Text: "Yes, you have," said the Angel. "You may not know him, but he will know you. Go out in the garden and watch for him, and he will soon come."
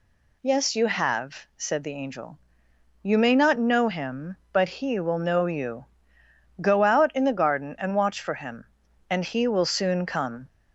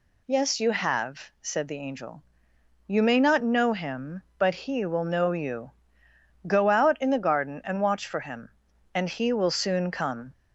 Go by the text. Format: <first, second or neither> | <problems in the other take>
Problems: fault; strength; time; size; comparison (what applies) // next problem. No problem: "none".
neither | none